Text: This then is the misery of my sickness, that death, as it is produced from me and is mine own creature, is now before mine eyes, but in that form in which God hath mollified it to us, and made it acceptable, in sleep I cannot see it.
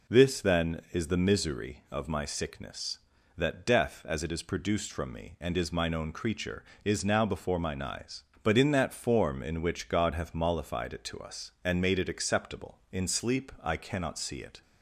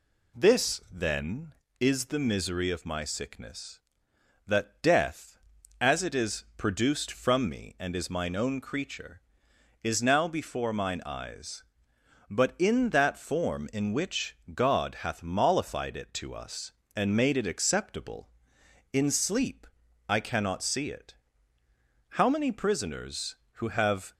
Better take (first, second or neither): first